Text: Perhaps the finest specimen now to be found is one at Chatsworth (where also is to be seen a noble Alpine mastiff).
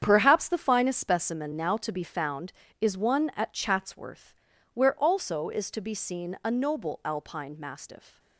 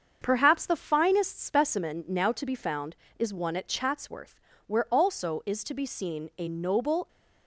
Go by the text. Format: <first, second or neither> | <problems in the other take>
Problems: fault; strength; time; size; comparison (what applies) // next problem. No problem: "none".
first | starts louder than the rest; until 1.2 s; 7 dB; strong in the first // stops before "Alpine mastiff"; at 7.0 s